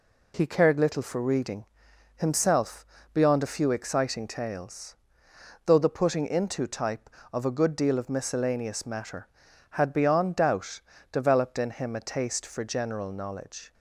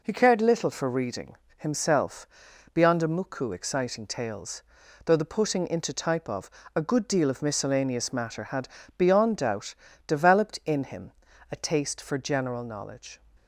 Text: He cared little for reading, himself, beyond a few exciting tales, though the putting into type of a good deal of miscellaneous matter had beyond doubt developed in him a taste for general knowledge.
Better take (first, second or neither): first